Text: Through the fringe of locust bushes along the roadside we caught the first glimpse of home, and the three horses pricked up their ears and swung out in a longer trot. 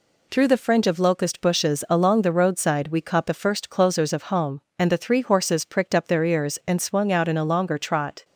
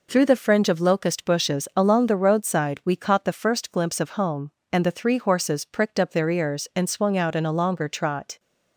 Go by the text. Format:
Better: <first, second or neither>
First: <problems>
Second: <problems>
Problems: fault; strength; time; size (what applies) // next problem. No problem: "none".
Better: second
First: says "closers" for "glimpse"; at 3.6 s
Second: none